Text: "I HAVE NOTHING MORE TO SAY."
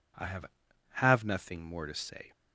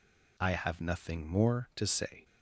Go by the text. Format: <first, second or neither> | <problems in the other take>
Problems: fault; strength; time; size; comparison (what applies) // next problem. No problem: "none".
second | says "HAVE" twice; at 0.9 s